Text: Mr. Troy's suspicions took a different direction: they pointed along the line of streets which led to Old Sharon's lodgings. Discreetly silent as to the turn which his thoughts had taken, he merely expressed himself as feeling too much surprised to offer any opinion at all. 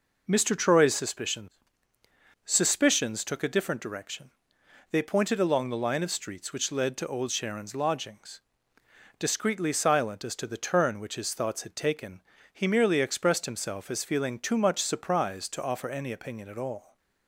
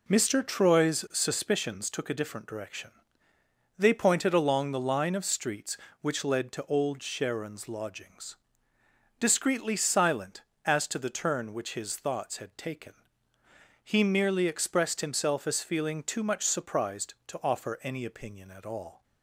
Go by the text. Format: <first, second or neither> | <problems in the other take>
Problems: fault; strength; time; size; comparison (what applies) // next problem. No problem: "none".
second | says "suspicions" twice; at 2.4 s